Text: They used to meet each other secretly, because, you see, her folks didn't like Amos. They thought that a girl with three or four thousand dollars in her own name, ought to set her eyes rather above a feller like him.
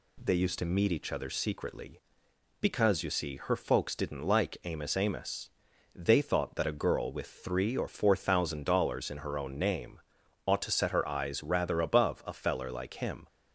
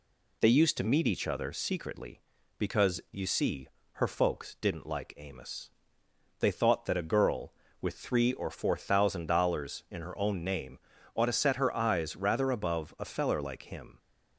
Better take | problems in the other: second | says "Amos" twice; at 4.9 s

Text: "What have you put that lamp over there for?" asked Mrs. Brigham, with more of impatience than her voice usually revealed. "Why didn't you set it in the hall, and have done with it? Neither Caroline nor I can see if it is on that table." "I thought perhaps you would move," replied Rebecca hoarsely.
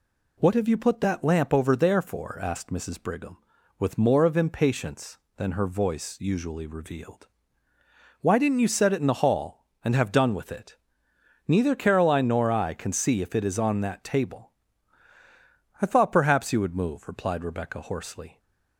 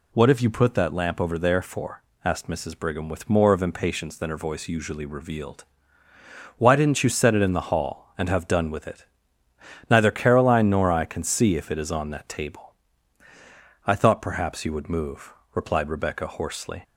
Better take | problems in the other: neither | none

